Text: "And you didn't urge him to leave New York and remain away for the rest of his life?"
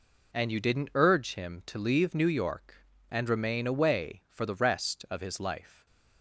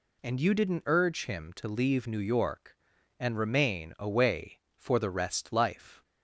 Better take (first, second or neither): first